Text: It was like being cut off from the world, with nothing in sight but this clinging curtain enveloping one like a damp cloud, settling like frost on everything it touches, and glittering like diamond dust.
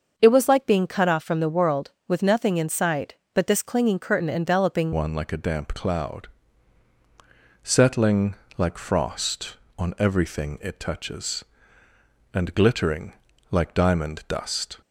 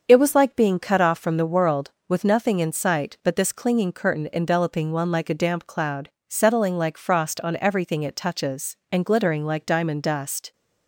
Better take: second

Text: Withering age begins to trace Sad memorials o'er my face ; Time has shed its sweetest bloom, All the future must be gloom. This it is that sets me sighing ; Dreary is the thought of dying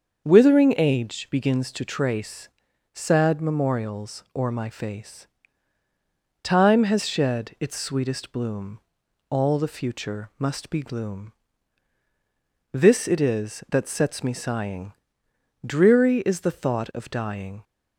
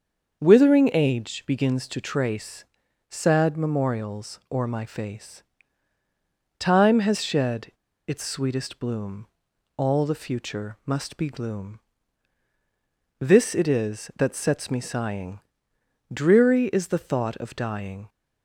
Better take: first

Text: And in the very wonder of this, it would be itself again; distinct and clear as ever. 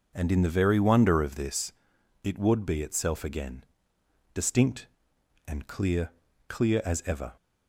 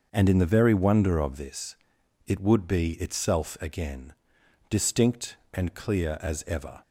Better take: second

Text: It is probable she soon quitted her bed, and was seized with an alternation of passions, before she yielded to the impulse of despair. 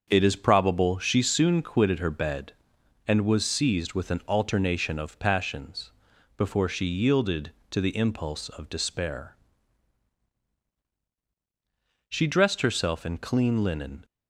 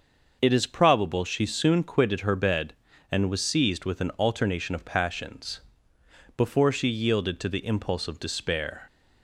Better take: second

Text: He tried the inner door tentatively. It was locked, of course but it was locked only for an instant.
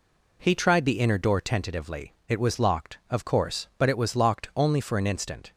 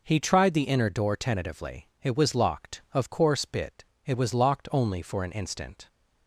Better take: first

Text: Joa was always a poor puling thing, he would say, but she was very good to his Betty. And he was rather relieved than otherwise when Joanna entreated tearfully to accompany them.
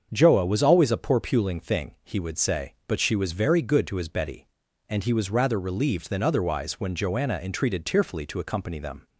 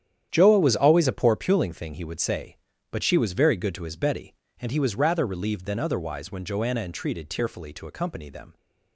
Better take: first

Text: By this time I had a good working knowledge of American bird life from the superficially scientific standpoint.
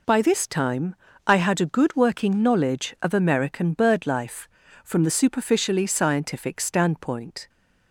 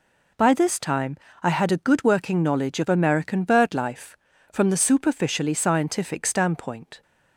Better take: neither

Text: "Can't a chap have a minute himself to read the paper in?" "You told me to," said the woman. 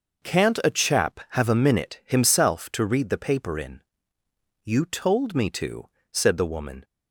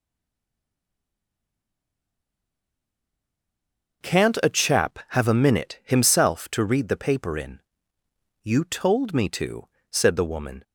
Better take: first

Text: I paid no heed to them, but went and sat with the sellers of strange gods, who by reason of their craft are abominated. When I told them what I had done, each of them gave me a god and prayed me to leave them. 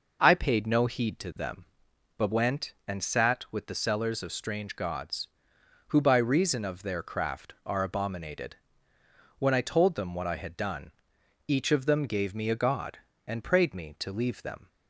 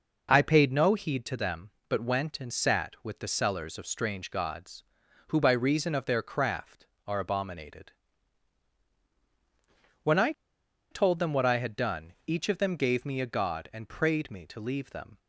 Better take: first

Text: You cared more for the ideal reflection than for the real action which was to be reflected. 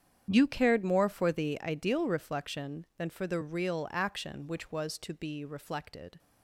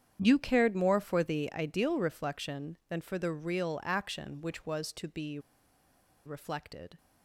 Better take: first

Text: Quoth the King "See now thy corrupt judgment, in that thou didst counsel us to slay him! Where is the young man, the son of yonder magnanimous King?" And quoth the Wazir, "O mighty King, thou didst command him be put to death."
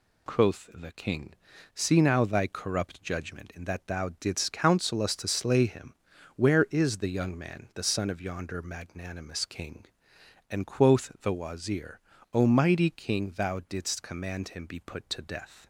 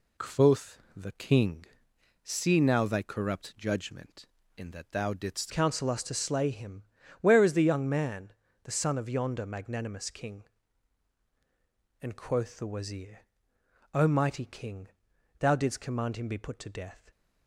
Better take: first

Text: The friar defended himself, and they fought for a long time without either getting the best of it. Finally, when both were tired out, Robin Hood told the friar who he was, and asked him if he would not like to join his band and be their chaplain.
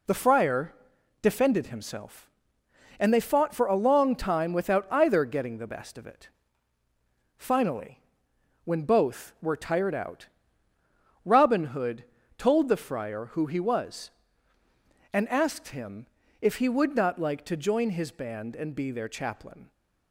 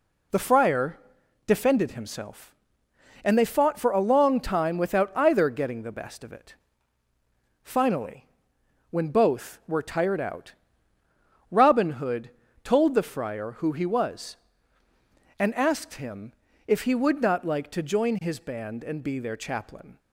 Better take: neither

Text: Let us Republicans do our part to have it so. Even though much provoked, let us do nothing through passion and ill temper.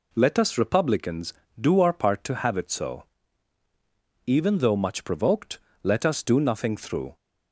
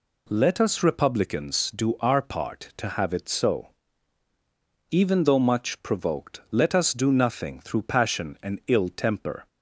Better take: second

